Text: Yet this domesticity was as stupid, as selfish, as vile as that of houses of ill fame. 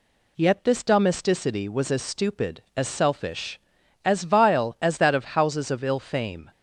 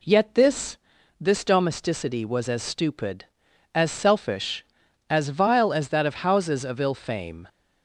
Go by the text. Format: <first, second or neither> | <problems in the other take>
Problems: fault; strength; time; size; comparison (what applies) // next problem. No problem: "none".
first | says "this" twice; at 1.2 s